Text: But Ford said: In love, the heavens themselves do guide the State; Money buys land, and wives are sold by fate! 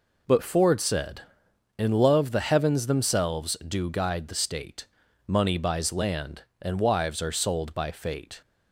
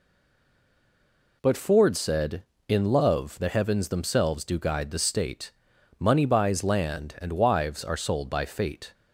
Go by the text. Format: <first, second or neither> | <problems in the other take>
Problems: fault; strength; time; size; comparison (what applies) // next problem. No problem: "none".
first | stays silent before the first word; noticeable; until 1.4 s; 1.4 s long